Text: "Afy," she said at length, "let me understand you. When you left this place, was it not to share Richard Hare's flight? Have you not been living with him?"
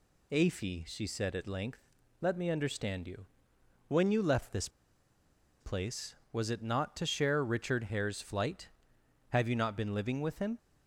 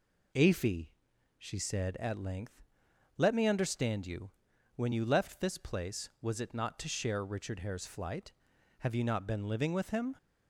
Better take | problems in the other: second | pauses between "this" and "place"; noticeable; at 4.6 s; 0.90 s long

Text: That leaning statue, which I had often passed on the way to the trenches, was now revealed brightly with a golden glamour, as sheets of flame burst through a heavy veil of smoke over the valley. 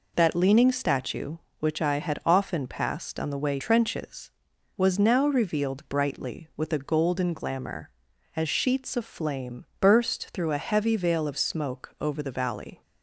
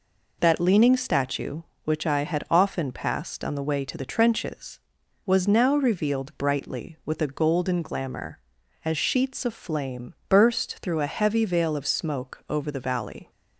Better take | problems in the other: second | skips "to the"; at 3.5 s

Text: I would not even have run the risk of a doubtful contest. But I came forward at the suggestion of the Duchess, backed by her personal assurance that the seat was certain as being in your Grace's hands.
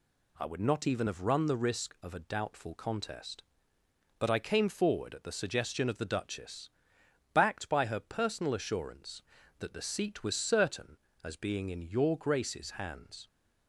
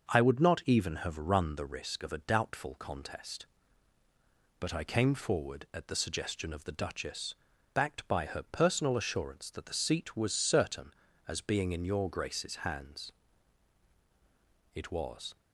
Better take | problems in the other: first | starts louder than the rest; noticeable; until 1.1 s; 6 dB // goes on to say "It was"; from 14.7 s on; 0.60 s long

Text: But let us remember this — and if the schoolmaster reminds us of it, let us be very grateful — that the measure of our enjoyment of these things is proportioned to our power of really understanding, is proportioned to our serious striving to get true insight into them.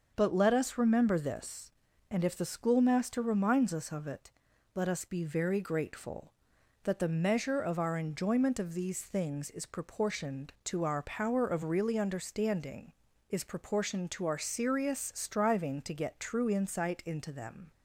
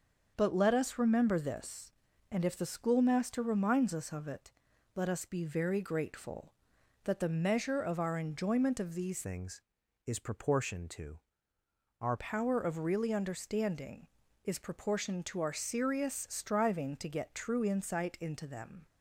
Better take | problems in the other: first | starts louder than the rest; until 1.3 s; 6.5 dB; also in the first // changes voice from "things" to "our"; from 9.2 to 12.1 s; 2.9 s long // pauses between "to" and "our"; noticeable; at 11.2 s; 0.80 s long

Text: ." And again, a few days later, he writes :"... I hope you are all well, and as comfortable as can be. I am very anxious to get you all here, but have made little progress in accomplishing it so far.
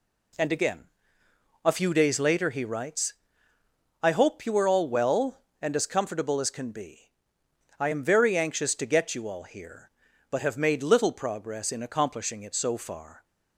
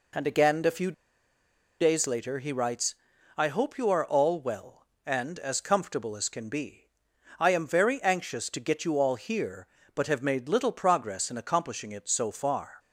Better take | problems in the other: first | pauses between "few" and "days"; noticeable; at 0.9 s; 0.88 s long

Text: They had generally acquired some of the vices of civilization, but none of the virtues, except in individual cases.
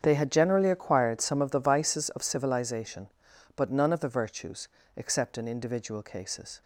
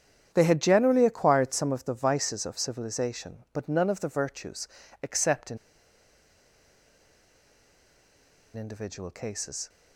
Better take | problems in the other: first | starts louder than the rest; strong; until 1.3 s; 9 dB; strong in the first // pauses between "in" and "individual"; strong; at 5.5 s; 2.9 s long

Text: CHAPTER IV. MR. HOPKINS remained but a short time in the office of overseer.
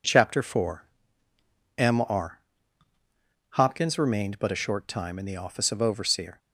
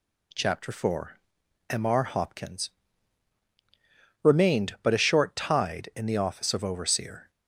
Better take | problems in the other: first | pauses between "HOPKINS" and "remained"; strong; at 2.6 s; 1.5 s long // says "tide" for "time"; at 5.3 s

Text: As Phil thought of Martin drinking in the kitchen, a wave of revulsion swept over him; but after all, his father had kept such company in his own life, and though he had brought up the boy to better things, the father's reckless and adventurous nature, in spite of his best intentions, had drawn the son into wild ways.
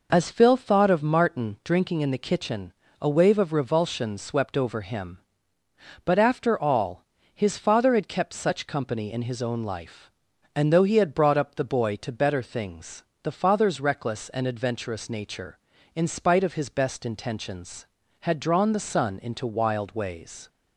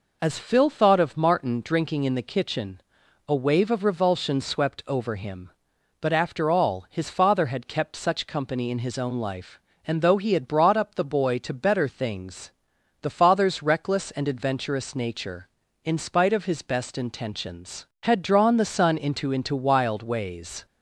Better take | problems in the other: first | says "into" twice; at 19.3 s

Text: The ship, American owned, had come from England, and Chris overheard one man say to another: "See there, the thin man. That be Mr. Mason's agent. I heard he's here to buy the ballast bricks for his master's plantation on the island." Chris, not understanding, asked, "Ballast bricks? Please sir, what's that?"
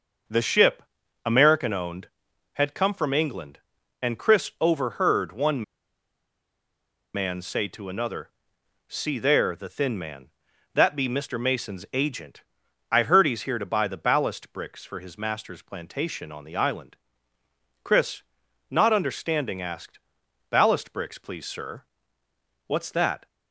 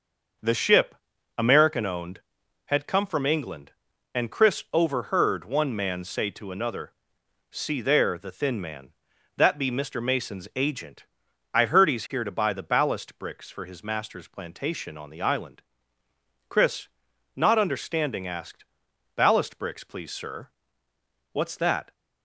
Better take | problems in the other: second | starts louder than the rest; until 1.7 s; 6 dB; also in the second // pauses between "one" and "man"; strong; at 5.6 s; 1.5 s long

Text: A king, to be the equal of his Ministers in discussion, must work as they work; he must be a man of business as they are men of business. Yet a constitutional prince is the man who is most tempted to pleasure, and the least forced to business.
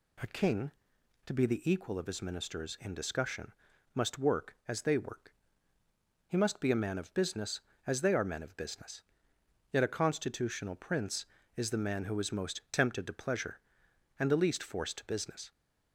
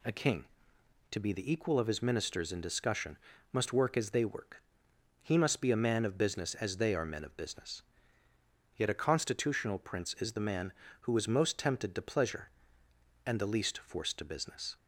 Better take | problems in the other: neither | none

